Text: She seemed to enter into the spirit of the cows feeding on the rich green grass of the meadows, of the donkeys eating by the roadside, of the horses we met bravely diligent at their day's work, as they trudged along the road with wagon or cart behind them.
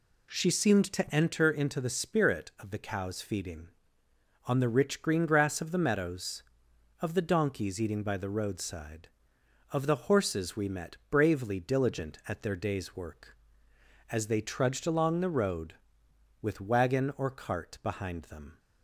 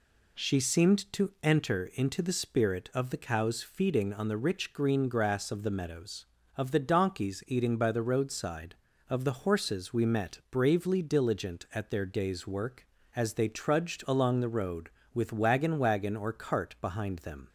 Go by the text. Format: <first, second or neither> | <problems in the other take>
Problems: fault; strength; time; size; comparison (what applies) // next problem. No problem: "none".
first | says "wagon" twice; at 15.7 s